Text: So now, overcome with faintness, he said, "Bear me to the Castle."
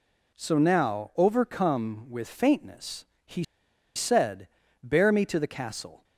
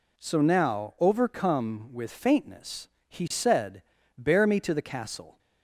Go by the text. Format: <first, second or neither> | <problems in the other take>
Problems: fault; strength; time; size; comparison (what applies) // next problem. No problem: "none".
second | pauses between "he" and "said"; noticeable; at 3.4 s; 0.52 s long